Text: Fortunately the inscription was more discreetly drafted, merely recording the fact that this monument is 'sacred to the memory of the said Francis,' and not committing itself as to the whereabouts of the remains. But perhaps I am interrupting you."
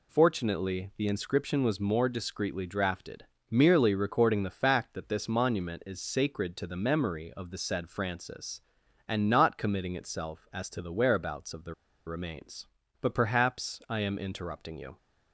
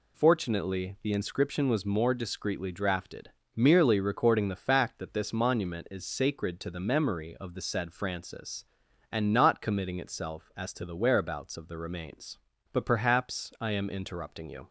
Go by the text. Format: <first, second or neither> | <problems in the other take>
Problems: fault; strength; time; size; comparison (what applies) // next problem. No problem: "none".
second | pauses between "the" and "remains"; slight; at 11.7 s; 0.34 s long